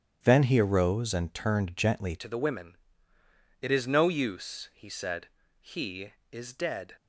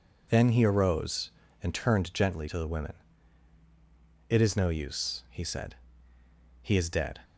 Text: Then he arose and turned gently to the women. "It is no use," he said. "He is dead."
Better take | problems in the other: second | starts louder than the rest; strong; until 1.2 s; 9.5 dB // changes voice at "to"; from 2.1 s on; 4.8 s long

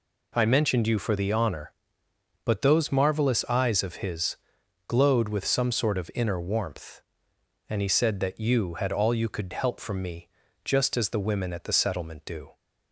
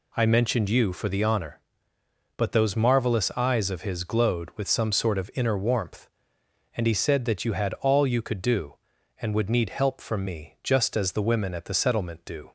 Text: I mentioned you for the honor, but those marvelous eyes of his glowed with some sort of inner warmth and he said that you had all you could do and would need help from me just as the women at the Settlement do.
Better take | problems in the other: second | pauses between "his" and "glowed"; noticeable; at 4.3 s; 0.52 s long // skips "do and would need"; at 9.5 s // pauses between "me" and "just"; slight; at 10.2 s; 0.36 s long

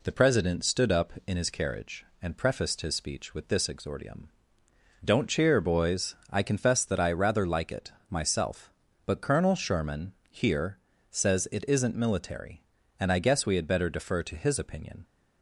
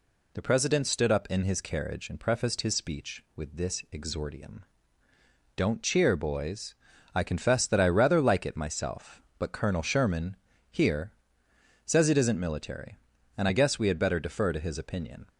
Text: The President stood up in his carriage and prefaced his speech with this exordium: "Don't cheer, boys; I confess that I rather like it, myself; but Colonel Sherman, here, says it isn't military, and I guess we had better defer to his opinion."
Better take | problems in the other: neither | none

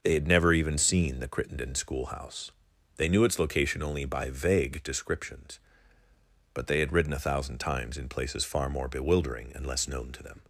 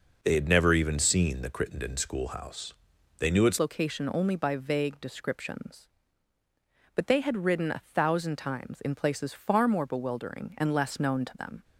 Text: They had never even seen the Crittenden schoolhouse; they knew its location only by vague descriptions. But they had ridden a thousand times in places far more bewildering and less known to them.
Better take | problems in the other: first | changes voice at "location"; from 3.5 s on; 8.1 s long

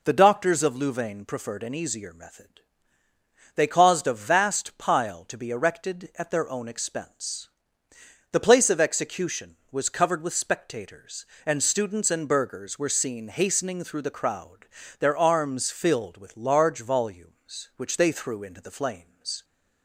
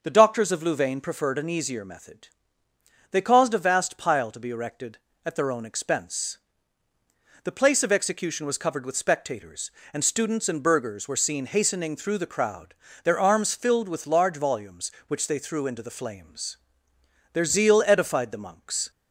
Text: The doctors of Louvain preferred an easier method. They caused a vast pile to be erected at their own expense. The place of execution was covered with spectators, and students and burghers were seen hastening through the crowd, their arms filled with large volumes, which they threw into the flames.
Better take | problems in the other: first | starts louder than the rest; until 1.0 s; 6 dB // goes on to say "Their zeal edified the monks"; from 17.3 s on; 1.5 s long

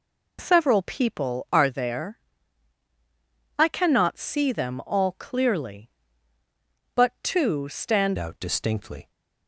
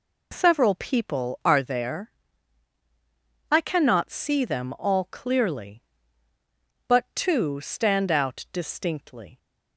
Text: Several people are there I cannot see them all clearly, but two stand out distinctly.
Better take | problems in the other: second | pauses between "there" and "I"; strong; at 2.1 s; 1.4 s long; strong in the second // changes voice at "out"; from 8.1 s on; 1.0 s long

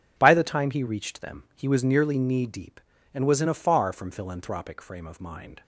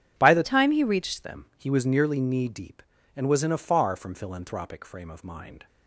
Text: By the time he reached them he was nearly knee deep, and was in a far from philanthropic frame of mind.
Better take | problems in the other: first | changes voice from "time" to "reached"; from 0.4 to 1.2 s; 0.8 s long

